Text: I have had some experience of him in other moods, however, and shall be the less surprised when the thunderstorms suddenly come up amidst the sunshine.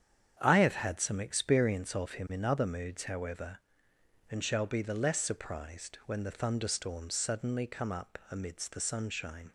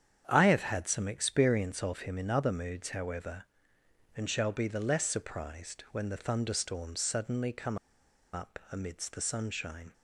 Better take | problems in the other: first | starts louder than the rest; strong; until 1.2 s; 8.5 dB; strong in the first // pauses between "come" and "up"; noticeable; at 7.7 s; 0.55 s long

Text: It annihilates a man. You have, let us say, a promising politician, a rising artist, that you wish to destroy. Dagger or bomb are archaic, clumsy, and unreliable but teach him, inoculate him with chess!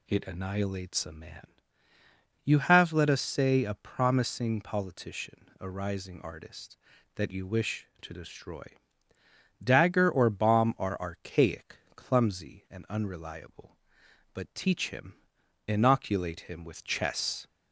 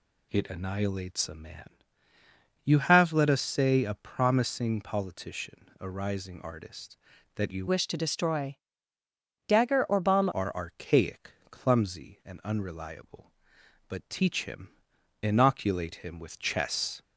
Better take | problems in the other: first | changes voice from "wish" to "bomb"; from 7.6 to 10.2 s; 2.6 s long

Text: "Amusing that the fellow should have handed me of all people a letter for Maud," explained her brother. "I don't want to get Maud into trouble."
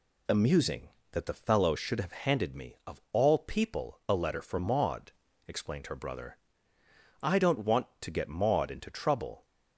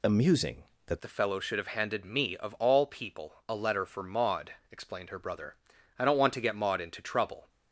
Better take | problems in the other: first | changes voice at "the"; from 1.0 s on; 6.4 s long

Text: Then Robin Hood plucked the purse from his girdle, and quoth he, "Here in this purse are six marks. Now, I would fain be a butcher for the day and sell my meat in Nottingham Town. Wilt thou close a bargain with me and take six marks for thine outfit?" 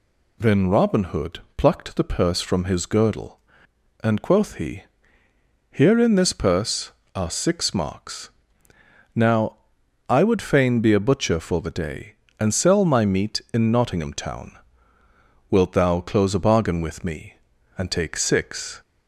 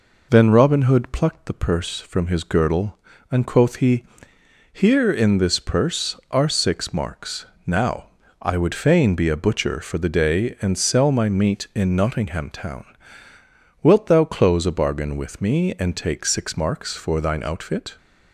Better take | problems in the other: second | pauses between "Hood" and "plucked"; slight; at 1.3 s; 0.16 s long // stops before "marks for thine outfit"; at 18.8 s

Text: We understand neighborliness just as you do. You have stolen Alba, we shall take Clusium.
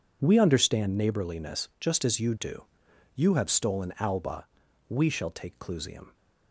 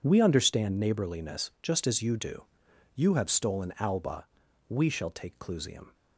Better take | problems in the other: neither | none

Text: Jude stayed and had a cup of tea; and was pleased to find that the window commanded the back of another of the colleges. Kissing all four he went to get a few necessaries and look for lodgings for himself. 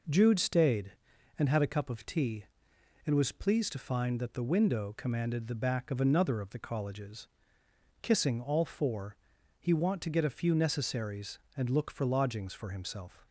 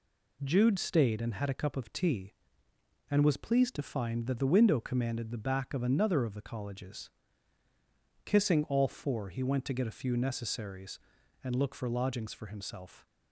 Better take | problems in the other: second | pauses between "four" and "he"; at 9.1 s; 0.42 s long // says "want" for "went"; at 9.7 s

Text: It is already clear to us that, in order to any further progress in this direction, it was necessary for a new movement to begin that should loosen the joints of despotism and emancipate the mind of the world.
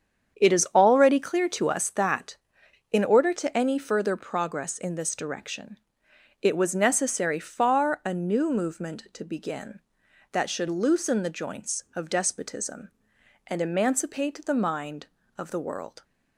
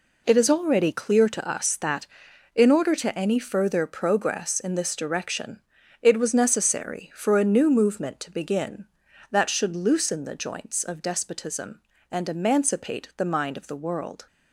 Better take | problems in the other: second | starts louder than the rest; strong; until 1.4 s; 8 dB // says "far" for "for"; at 7.3 s

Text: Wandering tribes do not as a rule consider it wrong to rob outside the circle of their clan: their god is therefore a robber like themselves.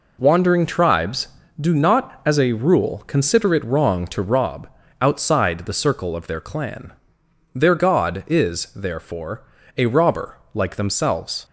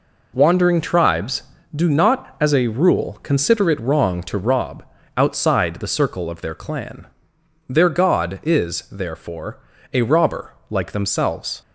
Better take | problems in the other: neither | pauses between "rob" and "outside"; slight; the same in both // pauses between "therefore" and "a"; slight; the same in both // pauses between "robber" and "like"; slight; the same in both

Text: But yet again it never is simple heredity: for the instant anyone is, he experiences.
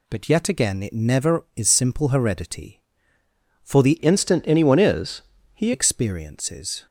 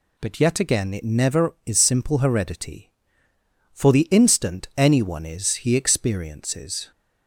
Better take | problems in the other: second | changes voice from "instant" to "he"; from 3.9 to 5.7 s; 1.8 s long

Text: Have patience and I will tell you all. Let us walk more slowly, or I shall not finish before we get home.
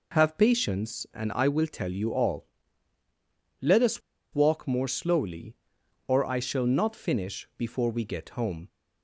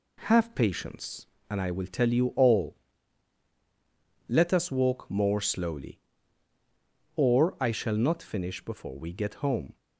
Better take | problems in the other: second | pauses between "us" and "walk"; slight; at 4.0 s; 0.32 s long

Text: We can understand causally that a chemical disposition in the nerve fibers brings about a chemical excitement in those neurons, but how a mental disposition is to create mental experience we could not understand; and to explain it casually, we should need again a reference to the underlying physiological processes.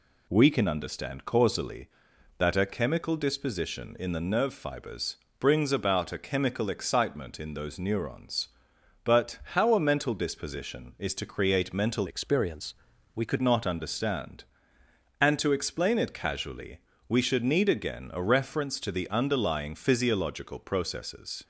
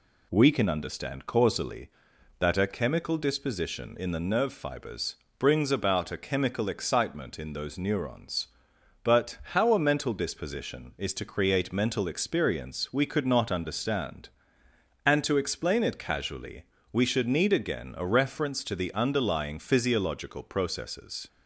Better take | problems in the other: second | pauses between "fibers" and "brings"; slight; at 5.1 s; 0.24 s long; slight in the second // pauses between "but" and "how"; slight; at 9.3 s; 0.16 s long; slight in the second // changes voice from "experience" to "could"; from 12.0 to 13.4 s; 1.4 s long // pauses between "experience" and "we"; at 12.7 s; 0.42 s long

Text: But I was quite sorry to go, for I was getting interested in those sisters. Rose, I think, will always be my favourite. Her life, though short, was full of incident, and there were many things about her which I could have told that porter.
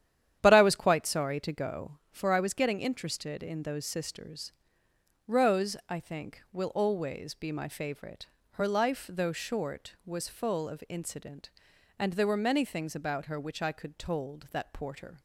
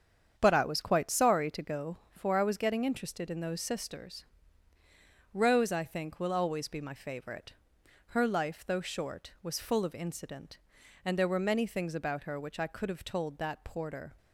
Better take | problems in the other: second | starts louder than the rest; strong; until 1.4 s; 10.5 dB; strong in the second // skips "have"; at 13.9 s

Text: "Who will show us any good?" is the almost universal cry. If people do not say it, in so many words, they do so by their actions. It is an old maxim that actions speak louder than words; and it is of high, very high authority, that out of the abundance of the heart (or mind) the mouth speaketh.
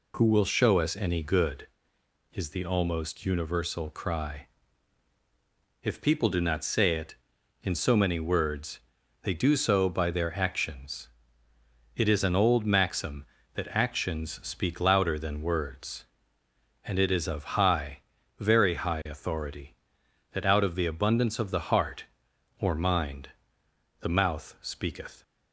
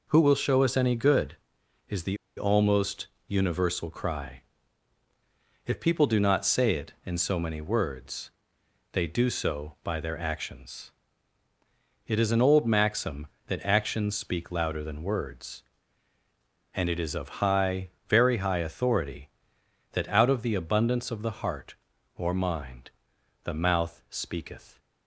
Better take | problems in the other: first | pauses between "the" and "almost"; slight; at 2.1 s; 0.21 s long // pauses between "almost" and "universal"; slight; at 3.0 s; 0.20 s long

